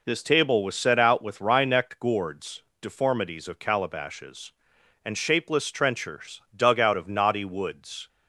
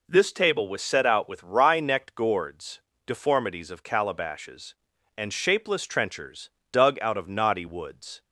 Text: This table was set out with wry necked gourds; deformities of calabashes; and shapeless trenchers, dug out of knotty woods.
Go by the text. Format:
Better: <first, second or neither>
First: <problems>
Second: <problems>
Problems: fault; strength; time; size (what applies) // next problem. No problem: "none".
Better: neither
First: none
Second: none